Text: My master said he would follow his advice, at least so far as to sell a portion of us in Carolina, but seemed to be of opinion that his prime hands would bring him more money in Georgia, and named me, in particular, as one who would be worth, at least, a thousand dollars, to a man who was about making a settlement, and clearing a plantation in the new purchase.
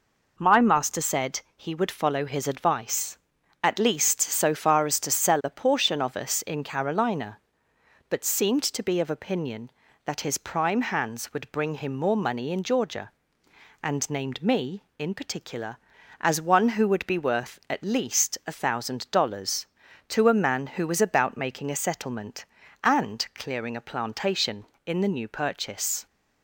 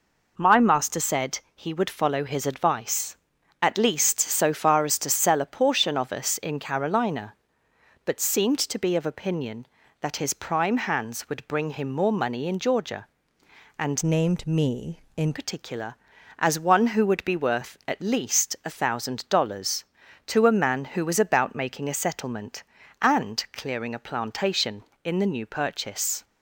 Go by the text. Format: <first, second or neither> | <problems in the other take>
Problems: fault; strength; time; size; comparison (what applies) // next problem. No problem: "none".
first | pauses between "said" and "he"; slight; at 1.3 s; 0.16 s long; slight in the first // changes voice from "named" to "in"; from 14.0 to 15.3 s; 1.3 s long